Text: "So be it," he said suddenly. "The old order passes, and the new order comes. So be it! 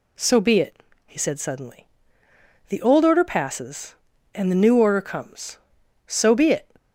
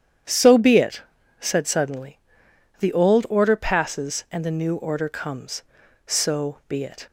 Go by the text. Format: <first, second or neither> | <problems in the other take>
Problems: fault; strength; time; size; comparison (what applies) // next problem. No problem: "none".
first | starts louder than the rest; strong; until 1.6 s; 9.5 dB // skips "he"; at 1.2 s